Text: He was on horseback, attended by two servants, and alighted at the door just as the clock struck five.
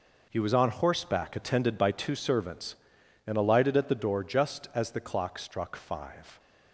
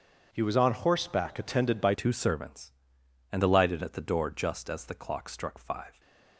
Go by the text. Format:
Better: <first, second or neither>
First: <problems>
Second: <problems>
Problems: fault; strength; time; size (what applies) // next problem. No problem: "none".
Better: first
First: none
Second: starts louder than the rest; strong; until 1.3 s; 7 dB // changes voice at "two"; from 1.9 s on; 4.0 s long